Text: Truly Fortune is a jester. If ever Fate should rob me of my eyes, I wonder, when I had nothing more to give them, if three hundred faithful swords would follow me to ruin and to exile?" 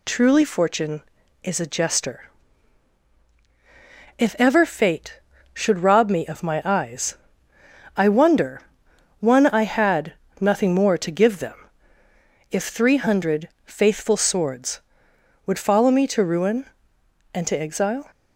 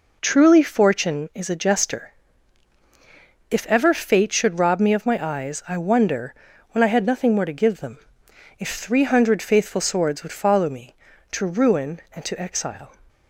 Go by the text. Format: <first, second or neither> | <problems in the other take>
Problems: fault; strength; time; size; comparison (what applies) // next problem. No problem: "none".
second | says "one" for "when"; at 9.2 s // pauses between "had" and "nothing"; slight; at 10.1 s; 0.28 s long // pauses between "hundred" and "faithful"; slight; at 13.4 s; 0.18 s long